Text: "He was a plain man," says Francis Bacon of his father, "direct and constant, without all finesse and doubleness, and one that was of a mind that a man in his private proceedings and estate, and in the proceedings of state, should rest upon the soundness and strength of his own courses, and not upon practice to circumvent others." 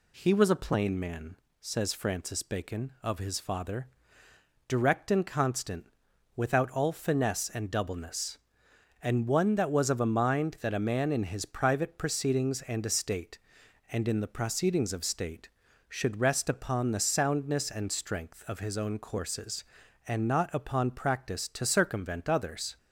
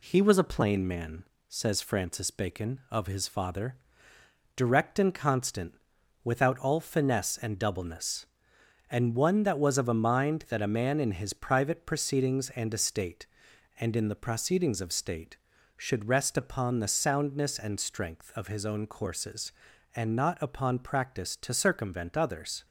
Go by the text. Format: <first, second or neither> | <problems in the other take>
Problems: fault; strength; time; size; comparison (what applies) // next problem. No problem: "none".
first | gets quieter; slight; throughout; 2.5 dB